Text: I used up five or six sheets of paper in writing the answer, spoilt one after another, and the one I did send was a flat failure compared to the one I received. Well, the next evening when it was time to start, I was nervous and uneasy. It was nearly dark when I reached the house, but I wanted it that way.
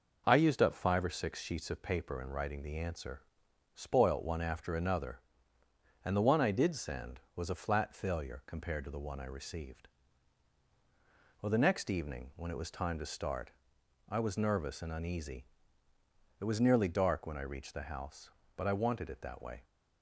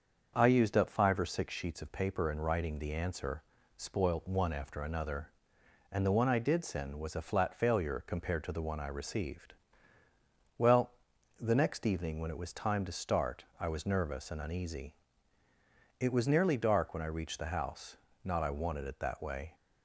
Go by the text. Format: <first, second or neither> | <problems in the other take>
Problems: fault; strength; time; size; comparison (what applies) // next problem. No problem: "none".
first | starts louder than the rest; until 1.3 s; 6.5 dB // says "not" for "but"; at 18.2 s